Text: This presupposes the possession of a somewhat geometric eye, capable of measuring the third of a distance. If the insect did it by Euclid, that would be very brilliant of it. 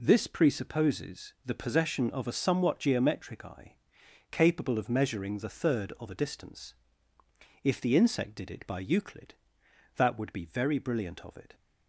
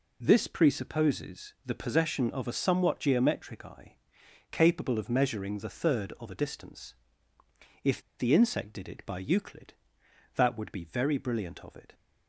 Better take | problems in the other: first | pauses between "If" and "the"; slight; at 8.0 s; 0.17 s long

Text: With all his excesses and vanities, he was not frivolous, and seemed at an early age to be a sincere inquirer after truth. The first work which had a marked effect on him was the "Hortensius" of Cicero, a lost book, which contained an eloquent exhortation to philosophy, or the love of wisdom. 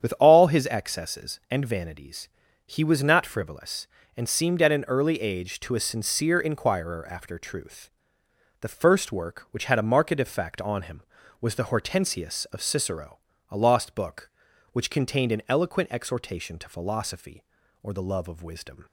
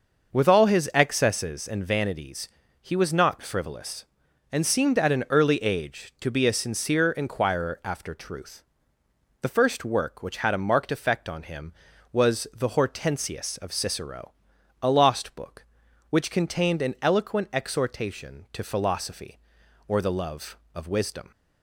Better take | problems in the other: second | starts louder than the rest; strong; until 1.1 s; 8.5 dB; noticeable in the second // skips "be"; at 5.7 s

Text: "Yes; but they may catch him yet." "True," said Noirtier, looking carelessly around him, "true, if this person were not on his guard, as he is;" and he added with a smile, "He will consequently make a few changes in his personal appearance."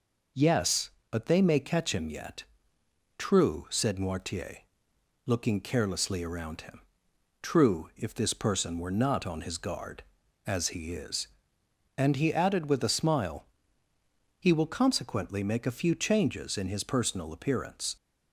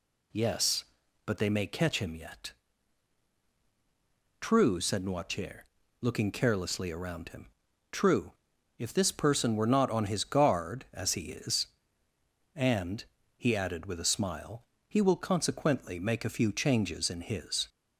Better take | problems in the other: first | pauses between "and" and "he"; slight; at 13.0 s; 0.34 s long // stops before "personal appearance"; at 17.6 s

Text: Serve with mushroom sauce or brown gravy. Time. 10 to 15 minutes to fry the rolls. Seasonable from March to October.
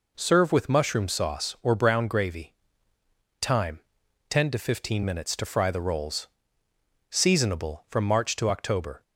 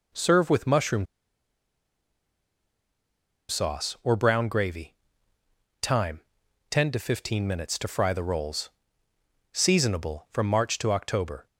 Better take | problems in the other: first | pauses between "mushroom" and "sauce"; strong; at 1.0 s; 2.4 s long

